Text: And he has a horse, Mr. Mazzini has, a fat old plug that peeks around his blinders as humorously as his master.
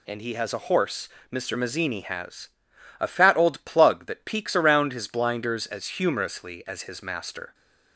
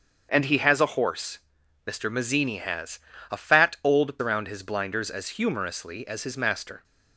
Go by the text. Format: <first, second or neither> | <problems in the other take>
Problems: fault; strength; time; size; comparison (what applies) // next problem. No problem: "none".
first | starts louder than the rest; until 1.3 s; 7 dB // skips "plug that peeks"; at 4.1 s